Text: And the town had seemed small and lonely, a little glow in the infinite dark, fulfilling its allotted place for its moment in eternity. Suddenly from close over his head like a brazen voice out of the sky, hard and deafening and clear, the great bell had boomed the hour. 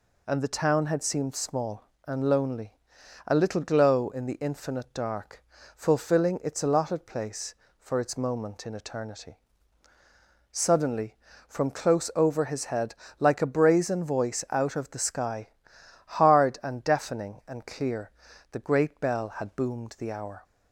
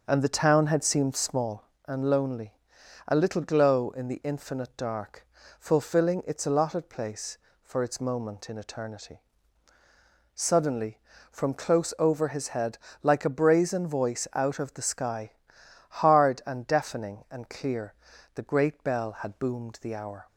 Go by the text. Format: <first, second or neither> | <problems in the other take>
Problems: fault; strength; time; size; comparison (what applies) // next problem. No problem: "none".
first | starts louder than the rest; until 1.6 s; 6 dB // pauses between "head" and "like"; slight; at 12.7 s; 0.26 s long; slight in the first